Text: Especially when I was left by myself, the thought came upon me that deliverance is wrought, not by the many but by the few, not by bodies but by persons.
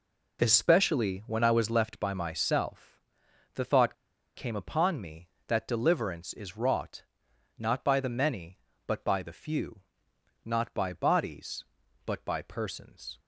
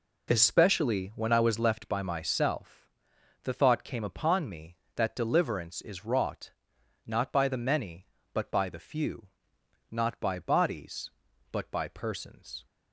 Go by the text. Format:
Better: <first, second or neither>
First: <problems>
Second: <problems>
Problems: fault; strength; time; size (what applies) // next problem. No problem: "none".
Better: second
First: pauses between "thought" and "came"; at 3.9 s; 0.41 s long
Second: none